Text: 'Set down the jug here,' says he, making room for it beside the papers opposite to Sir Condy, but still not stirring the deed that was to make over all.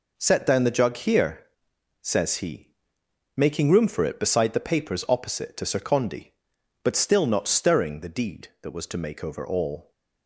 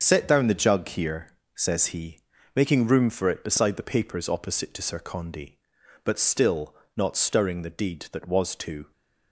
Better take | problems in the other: first | starts louder than the rest; until 1.0 s; 7 dB // pauses between "still" and "not"; slight; at 6.7 s; 0.22 s long // stops before "make over all"; at 8.9 s

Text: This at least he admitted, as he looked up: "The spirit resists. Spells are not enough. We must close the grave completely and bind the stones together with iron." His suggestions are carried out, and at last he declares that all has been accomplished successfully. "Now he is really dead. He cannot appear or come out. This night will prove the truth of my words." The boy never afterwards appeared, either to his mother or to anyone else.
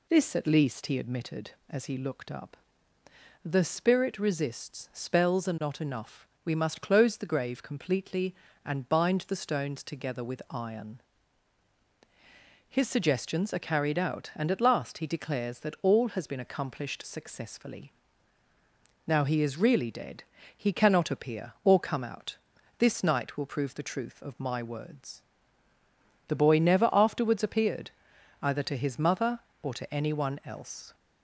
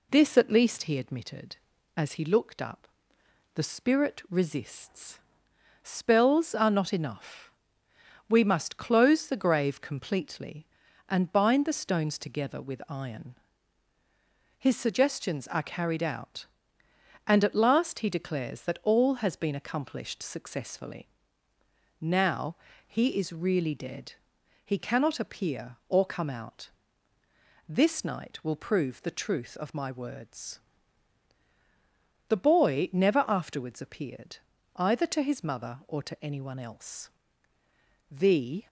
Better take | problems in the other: first | pauses between "Now" and "he"; slight; at 22.5 s; 0.32 s long // goes on to say "The"; from 38.0 s on; 0.58 s long

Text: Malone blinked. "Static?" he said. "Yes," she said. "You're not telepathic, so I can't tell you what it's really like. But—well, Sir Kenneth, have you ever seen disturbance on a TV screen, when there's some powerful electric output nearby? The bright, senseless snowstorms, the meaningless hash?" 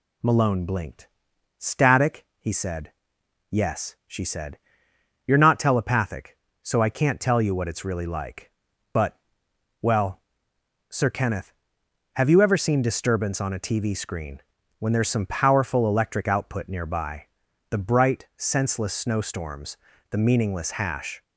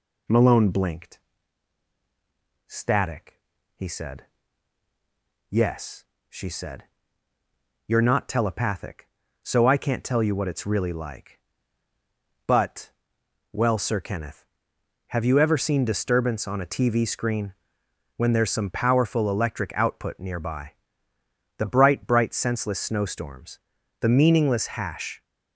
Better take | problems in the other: first | says "bright" twice; at 22.0 s

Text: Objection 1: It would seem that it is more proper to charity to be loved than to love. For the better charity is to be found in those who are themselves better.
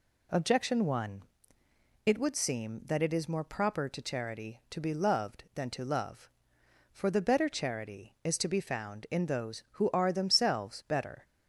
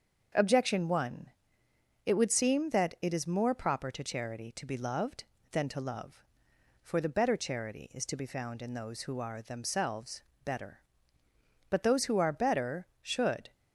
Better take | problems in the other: first | starts louder than the rest; until 2.1 s; 7 dB // pauses between "themselves" and "better"; slight; at 10.2 s; 0.20 s long // goes on to say "But those who are better should"; strong; from 11.6 s on; 1.8 s long

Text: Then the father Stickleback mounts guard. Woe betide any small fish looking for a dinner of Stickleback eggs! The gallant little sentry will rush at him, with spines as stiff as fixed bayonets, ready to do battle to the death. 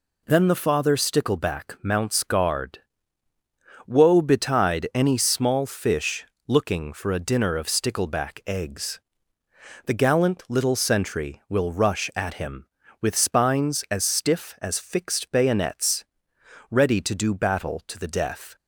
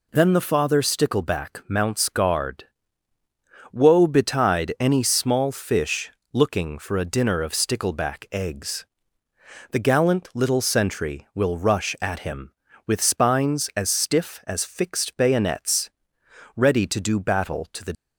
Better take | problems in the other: first | pauses between "fish" and "looking"; slight; at 6.1 s; 0.22 s long; slight in the first // stops before "death"; at 17.9 s

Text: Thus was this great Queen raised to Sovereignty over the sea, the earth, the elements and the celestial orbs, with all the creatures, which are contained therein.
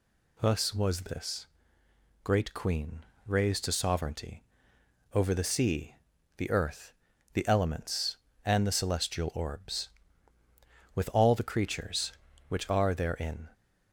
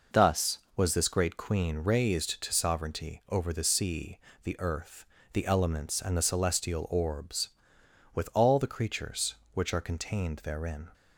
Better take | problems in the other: second | pauses between "this" and "great"; noticeable; at 1.4 s; 0.76 s long // pauses between "Queen" and "raised"; slight; at 3.0 s; 0.20 s long // pauses between "Sovereignty" and "over"; noticeable; at 4.4 s; 0.72 s long // skips "contained"; at 12.9 s

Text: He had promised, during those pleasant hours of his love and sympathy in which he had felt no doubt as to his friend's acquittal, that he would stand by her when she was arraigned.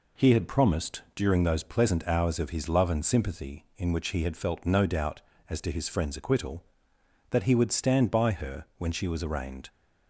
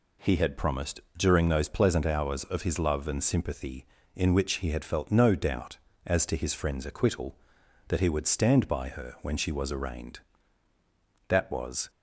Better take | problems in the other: first | goes on to say "That was"; from 11.2 s on; 0.60 s long

